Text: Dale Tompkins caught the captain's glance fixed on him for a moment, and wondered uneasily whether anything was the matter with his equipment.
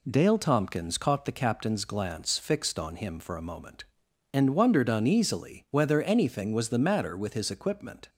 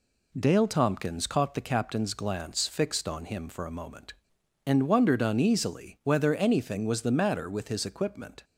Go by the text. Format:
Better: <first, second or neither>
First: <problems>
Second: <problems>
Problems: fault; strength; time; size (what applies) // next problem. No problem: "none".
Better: neither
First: none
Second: none